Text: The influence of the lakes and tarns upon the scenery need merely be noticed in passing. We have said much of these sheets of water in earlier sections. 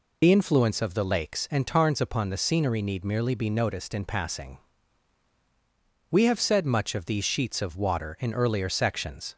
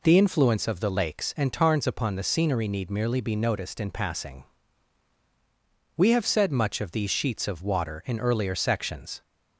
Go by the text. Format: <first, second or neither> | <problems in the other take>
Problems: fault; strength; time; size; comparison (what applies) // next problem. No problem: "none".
second | loses the start of "The"; at 0.2 s; 50 ms